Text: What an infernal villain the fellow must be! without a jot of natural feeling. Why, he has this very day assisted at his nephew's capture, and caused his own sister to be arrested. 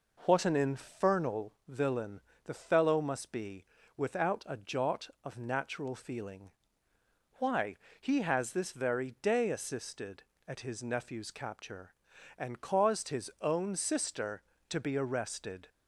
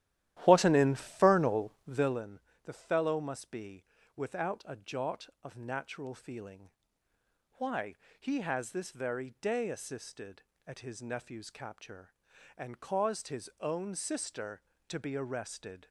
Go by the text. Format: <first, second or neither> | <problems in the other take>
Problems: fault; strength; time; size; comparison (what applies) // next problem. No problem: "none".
first | starts louder than the rest; strong; until 2.3 s; 13 dB // pauses between "infernal" and "villain"; slight; at 1.7 s; 0.16 s long; slight in the first // pauses between "villain" and "the"; slight; at 2.3 s; 0.24 s long; slight in the first